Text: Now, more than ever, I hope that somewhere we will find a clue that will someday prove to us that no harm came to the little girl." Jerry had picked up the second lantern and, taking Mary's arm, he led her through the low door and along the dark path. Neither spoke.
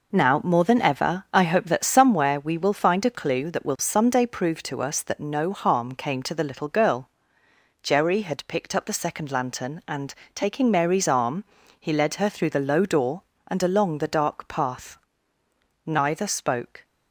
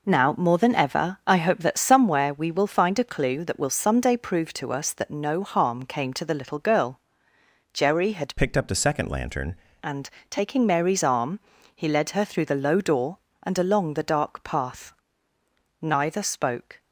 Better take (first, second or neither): first